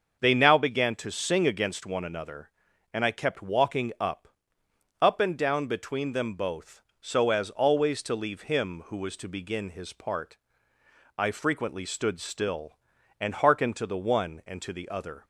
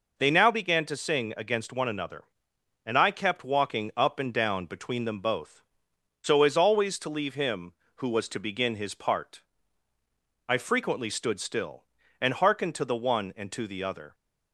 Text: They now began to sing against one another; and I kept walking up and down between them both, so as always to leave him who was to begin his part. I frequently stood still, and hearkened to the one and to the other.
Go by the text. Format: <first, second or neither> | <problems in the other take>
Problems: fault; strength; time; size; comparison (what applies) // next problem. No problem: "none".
second | starts louder than the rest; until 1.2 s; 6.5 dB // says "up" twice; at 5.0 s